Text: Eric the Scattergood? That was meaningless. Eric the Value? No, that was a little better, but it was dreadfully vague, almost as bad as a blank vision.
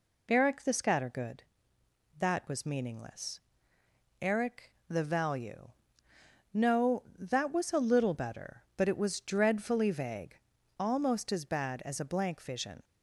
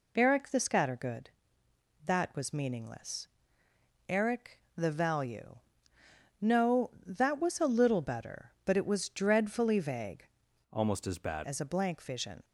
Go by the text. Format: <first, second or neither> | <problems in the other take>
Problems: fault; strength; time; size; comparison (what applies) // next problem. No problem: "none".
first | pauses between "Eric" and "the"; slight; at 4.5 s; 0.18 s long; slight in the first // changes voice from "almost" to "bad"; from 10.7 to 11.4 s; 0.7 s long